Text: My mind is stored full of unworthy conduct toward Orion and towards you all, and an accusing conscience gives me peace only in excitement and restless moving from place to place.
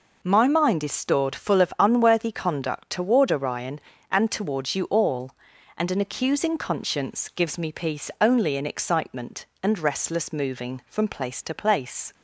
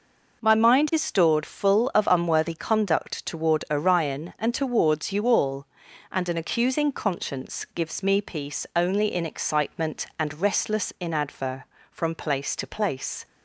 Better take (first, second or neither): first